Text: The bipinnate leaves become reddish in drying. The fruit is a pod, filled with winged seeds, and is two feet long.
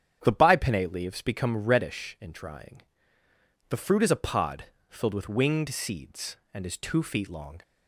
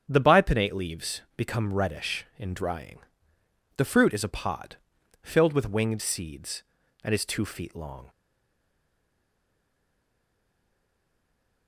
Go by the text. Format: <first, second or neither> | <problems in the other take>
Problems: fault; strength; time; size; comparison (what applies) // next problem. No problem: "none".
first | starts louder than the rest; strong; until 1.0 s; 8.5 dB; strong in the first // stays silent after the last word; strong; from 8.0 s on; 3.6 s long